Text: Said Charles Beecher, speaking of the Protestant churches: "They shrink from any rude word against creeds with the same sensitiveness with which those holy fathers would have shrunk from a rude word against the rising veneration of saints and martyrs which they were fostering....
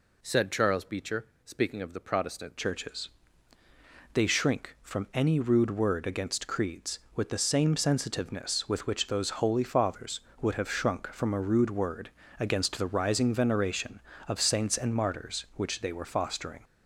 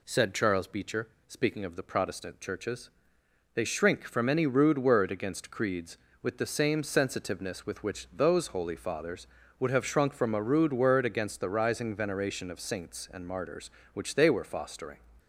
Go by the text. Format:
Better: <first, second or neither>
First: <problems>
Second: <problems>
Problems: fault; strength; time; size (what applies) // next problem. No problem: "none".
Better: second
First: changes voice at "churches"; from 2.5 s on; 14.1 s long // pauses between "word" and "against"; slight; at 12.0 s; 0.30 s long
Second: none